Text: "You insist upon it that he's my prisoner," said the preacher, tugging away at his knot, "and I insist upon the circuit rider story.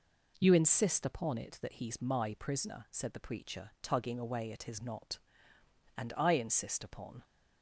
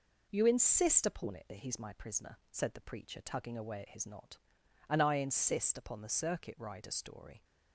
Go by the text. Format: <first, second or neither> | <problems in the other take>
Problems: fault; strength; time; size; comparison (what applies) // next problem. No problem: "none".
second | stops before "the circuit rider story"; at 7.2 s